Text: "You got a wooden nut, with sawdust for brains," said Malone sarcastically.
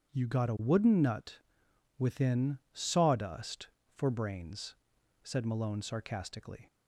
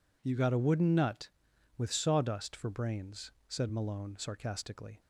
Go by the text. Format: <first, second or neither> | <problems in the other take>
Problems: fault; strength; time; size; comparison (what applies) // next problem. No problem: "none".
second | starts louder than the rest; strong; until 1.1 s; 8 dB // says "within" for "with"; at 1.9 s